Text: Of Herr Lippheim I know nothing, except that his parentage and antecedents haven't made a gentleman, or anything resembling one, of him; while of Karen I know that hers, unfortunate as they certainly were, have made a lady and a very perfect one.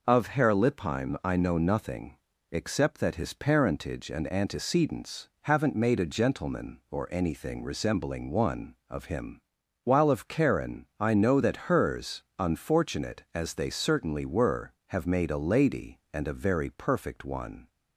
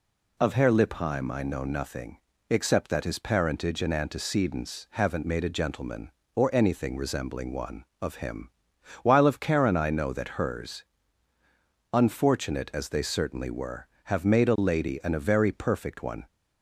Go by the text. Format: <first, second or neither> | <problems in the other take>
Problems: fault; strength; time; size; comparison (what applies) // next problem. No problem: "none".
neither | none